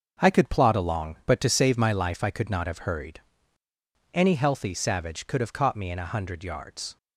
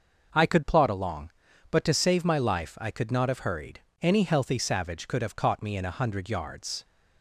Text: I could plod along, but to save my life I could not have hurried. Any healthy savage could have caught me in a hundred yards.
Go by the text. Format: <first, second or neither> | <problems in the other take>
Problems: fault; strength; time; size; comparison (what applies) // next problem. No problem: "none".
second | gets quieter; strong; throughout; 8.5 dB